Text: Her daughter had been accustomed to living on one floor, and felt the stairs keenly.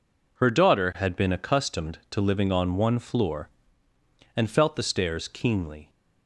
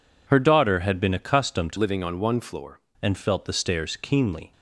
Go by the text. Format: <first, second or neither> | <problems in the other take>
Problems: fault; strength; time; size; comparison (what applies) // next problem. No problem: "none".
first | changes voice from "living" to "floor"; from 1.7 to 2.7 s; 1.0 s long